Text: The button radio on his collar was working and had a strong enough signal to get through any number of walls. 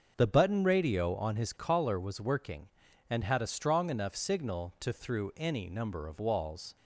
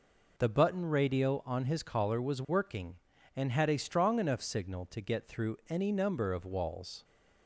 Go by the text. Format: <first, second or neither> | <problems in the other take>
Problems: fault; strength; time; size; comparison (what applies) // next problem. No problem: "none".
second | starts louder than the rest; until 1.1 s; 6.5 dB // skips "get"; at 4.9 s